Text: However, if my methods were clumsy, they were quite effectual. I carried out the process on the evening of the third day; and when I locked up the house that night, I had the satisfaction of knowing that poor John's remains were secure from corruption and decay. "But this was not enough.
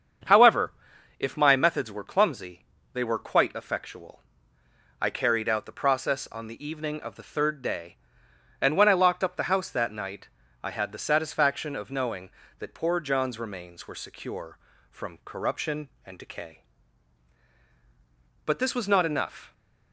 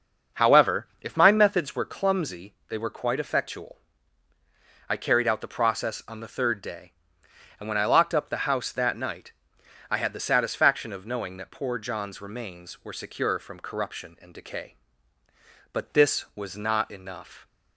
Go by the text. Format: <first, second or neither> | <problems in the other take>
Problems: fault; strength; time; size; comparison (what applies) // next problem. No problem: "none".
first | starts louder than the rest; until 1.4 s; 6.5 dB; strong in the first // skips "evening of the"; at 6.2 s